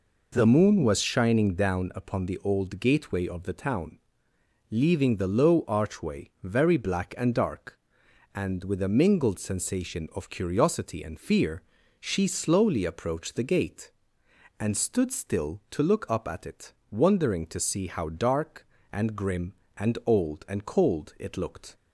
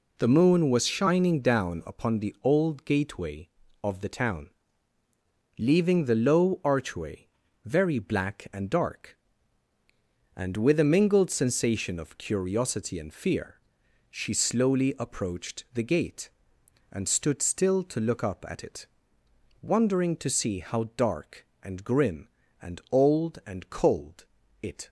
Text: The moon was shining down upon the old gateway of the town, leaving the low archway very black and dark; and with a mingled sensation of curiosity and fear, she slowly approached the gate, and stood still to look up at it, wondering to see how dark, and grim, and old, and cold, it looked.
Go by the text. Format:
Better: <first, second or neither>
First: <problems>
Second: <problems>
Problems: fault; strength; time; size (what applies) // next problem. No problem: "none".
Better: first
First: none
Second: pauses between "archway" and "very"; at 7.2 s; 0.38 s long // stops before "looked"; at 24.8 s